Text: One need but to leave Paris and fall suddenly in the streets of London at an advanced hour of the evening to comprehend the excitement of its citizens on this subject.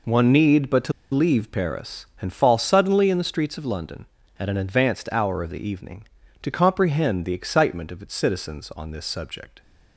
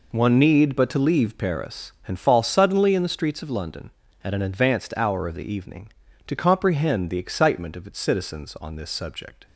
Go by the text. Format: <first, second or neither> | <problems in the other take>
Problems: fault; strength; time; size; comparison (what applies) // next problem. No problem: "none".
second | pauses between "to" and "leave"; slight; at 0.9 s; 0.21 s long